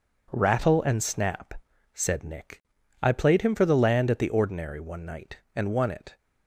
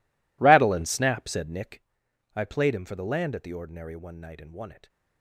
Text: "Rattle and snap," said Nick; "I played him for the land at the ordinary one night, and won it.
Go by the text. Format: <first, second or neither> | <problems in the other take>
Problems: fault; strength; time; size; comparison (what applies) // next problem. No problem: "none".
first | gets quieter; strong; throughout; 19.5 dB